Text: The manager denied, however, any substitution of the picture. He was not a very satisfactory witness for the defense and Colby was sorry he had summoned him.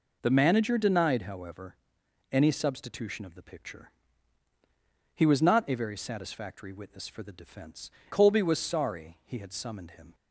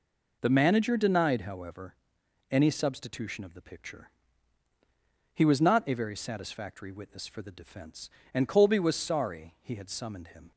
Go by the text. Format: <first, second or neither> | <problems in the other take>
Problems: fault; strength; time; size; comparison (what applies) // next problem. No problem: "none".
second | skips "and"; at 8.0 s